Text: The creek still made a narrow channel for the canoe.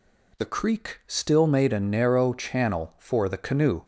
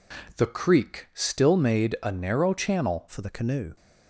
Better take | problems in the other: first | changes voice at "for"; from 3.0 s on; 0.7 s long

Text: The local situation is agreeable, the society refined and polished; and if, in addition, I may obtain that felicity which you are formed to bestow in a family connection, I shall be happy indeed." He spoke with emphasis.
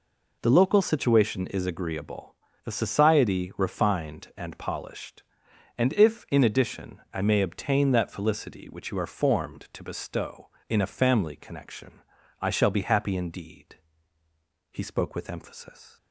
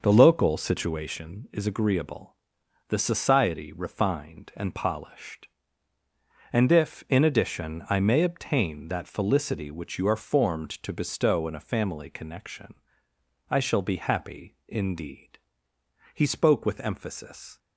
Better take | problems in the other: first | starts louder than the rest; noticeable; until 1.2 s; 6 dB

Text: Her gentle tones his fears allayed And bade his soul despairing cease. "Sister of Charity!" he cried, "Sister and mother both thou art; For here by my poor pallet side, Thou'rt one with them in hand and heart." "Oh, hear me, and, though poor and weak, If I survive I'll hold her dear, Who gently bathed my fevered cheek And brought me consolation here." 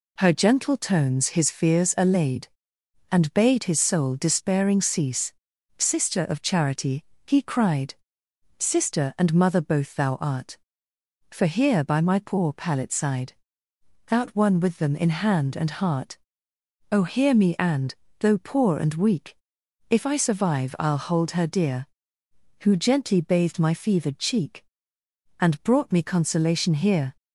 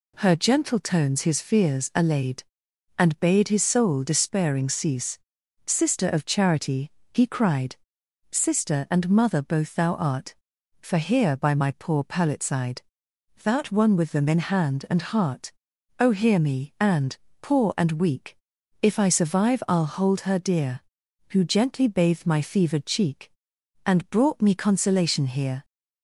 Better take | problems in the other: first | skips "though"; at 17.2 s

